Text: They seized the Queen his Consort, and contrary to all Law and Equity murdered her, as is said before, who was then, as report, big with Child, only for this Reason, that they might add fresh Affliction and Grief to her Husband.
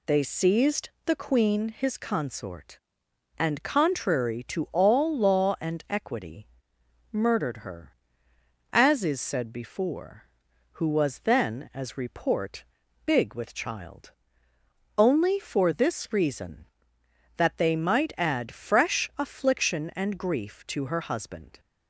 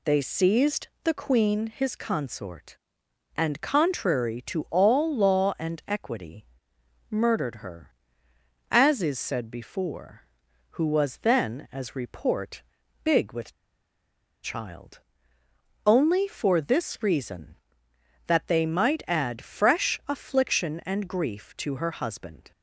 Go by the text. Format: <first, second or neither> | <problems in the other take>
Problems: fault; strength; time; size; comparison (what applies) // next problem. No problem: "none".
first | pauses between "seized" and "the"; slight; at 0.8 s; 0.16 s long; slight in the first // pauses between "Equity" and "murdered"; noticeable; at 6.4 s; 0.64 s long; noticeable in the first // pauses between "with" and "Child"; noticeable; at 13.5 s; 0.91 s long